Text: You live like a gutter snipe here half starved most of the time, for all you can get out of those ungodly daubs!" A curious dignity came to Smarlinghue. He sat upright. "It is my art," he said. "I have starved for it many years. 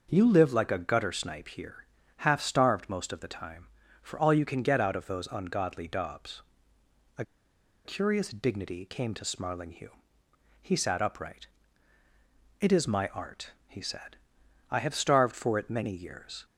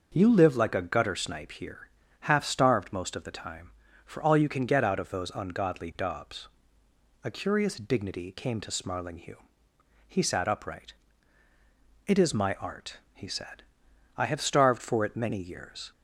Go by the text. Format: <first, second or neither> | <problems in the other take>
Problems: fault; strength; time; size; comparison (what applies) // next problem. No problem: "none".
second | pauses between "here" and "half"; at 1.8 s; 0.38 s long; also in the second // pauses between "A" and "curious"; noticeable; at 7.2 s; 0.61 s long